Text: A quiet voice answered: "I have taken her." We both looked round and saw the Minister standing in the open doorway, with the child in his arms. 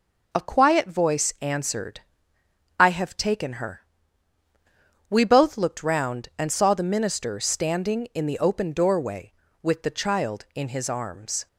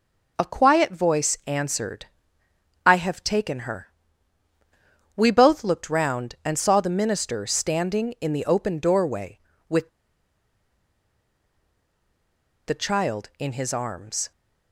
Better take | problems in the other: first | pauses between "with" and "the"; strong; at 9.8 s; 2.7 s long

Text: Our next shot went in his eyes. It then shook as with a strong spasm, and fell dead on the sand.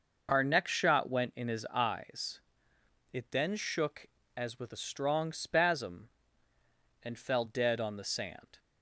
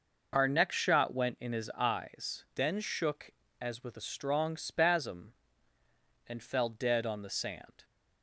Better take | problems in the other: first | skips "It"; at 2.4 s

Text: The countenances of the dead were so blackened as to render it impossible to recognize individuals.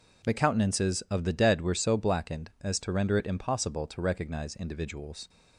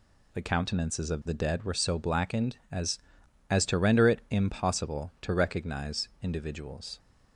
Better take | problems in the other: first | says "as" twice; at 3.4 s

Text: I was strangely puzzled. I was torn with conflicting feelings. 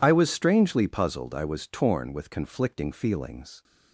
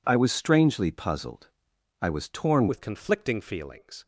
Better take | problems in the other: first | changes voice at "with"; from 2.6 s on; 1.4 s long

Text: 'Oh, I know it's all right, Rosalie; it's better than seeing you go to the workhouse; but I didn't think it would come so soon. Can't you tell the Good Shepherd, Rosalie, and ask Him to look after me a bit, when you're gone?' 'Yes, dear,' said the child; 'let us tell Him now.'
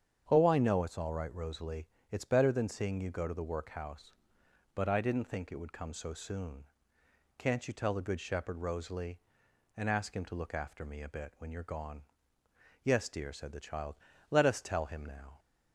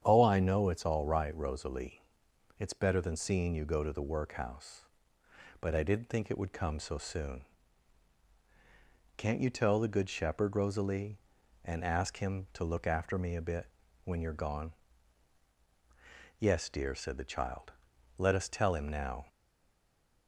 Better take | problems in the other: first | starts louder than the rest; strong; until 1.0 s; 8.5 dB; strong in the first // stays silent after the last word; from 19.2 s on; 1.0 s long

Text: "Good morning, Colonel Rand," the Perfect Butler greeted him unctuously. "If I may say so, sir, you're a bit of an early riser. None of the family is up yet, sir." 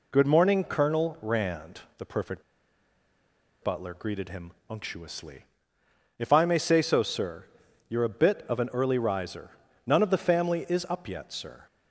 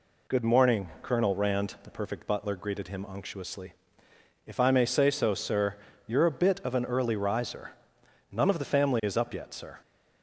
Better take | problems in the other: second | pauses between "Perfect" and "Butler"; at 2.4 s; 1.1 s long // pauses between "him" and "unctuously"; slight; at 4.4 s; 0.18 s long

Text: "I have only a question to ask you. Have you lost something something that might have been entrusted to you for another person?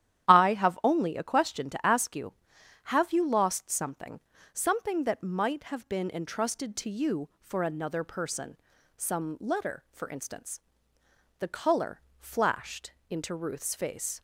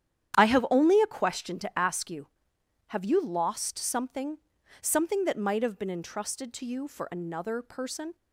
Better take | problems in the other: second | starts louder than the rest; strong; until 1.3 s; 11 dB; strong in the second // pauses between "something" and "something"; slight; at 4.2 s; 0.32 s long; also in the second // goes on to say "Some letter for instance The color flashed into Ruth's face"; strong; from 8.9 s on; 5.2 s long

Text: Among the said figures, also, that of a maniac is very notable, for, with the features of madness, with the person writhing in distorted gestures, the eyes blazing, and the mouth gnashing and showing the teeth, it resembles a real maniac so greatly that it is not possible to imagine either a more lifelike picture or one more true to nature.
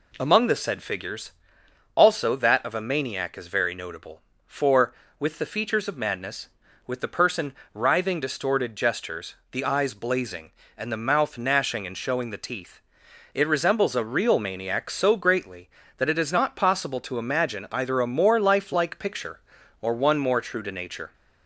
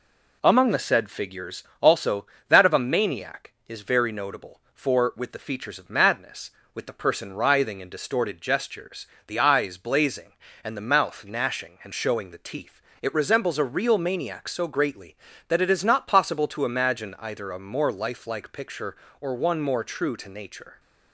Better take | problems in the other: second | pauses between "person" and "writhing"; slight; at 7.5 s; 0.22 s long // skips "in"; at 8.1 s

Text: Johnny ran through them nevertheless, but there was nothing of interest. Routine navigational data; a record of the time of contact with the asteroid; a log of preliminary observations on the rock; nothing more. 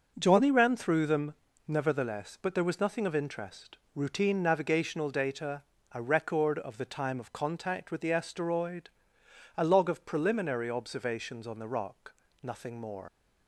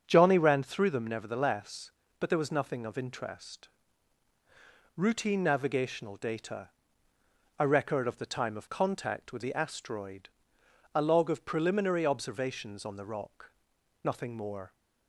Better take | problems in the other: second | starts louder than the rest; until 1.1 s; 6.5 dB; also in the second // pauses between "them" and "nevertheless"; slight; at 1.3 s; 0.34 s long // leaves "more" unfinished; at 13.0 s; 115 ms

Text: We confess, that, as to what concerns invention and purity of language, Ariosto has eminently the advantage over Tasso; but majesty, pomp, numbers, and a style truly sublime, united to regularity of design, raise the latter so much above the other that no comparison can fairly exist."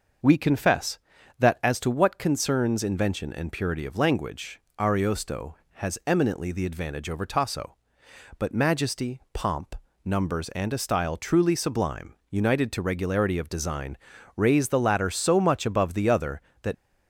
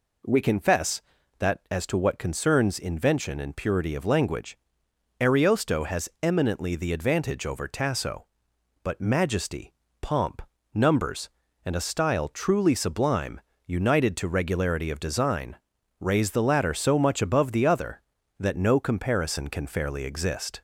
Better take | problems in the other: second | starts louder than the rest; noticeable; until 1.6 s; 6 dB // stops before "no comparison can fairly exist"; at 16.7 s

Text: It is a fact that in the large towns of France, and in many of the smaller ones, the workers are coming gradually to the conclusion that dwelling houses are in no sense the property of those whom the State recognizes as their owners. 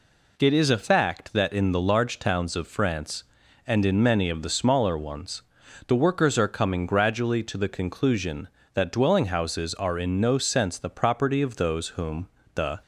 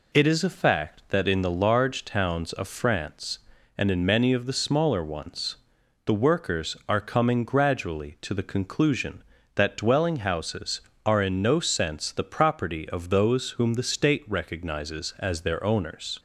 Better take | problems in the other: second | pauses between "whom" and "the"; slight; at 12.2 s; 0.28 s long // stops before "State recognizes as their owners"; at 12.8 s

